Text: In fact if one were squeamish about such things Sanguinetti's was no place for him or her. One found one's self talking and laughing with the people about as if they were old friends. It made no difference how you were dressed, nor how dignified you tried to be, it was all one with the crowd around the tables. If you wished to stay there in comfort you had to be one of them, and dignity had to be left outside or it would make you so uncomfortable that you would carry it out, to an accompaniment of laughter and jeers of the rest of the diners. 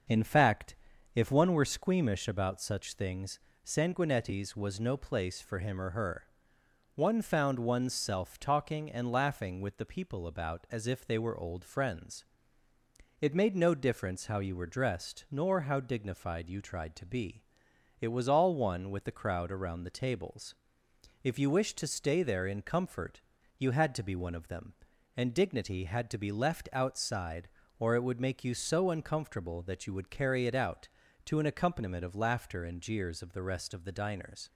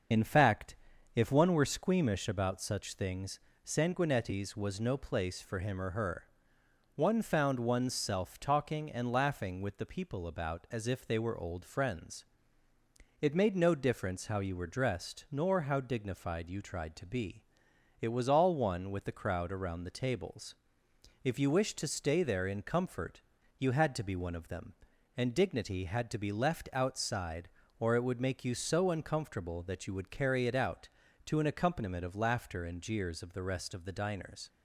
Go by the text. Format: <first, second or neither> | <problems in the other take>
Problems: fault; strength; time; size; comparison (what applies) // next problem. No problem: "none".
first | loses the start of "In"; at 0.1 s; 35 ms // starts louder than the rest; until 1.5 s; 6.5 dB; also in the first // pauses between "fact" and "if"; at 0.7 s; 0.40 s long; also in the first // pauses between "things" and "Sanguinetti's"; slight; at 3.3 s; 0.26 s long; slight in the first // pauses between "comfort" and "you"; at 23.2 s; 0.38 s long; also in the first